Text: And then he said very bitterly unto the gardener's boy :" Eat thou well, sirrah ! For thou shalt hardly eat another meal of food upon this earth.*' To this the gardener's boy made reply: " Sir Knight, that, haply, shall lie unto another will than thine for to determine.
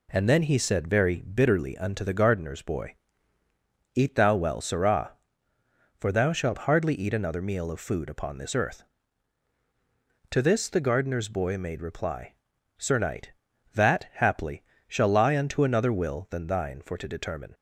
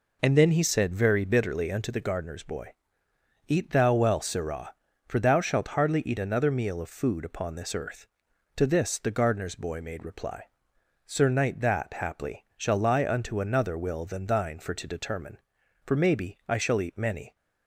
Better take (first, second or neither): first